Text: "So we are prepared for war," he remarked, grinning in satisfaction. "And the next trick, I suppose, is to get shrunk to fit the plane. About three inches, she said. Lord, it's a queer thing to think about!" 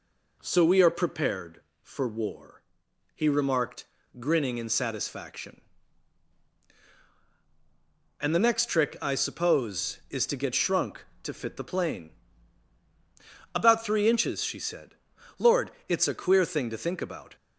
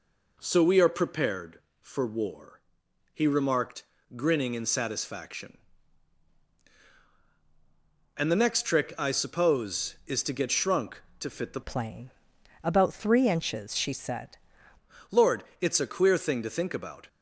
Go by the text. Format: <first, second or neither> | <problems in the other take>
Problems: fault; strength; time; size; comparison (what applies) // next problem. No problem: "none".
first | changes voice from "plane" to "said"; from 11.6 to 14.3 s; 2.7 s long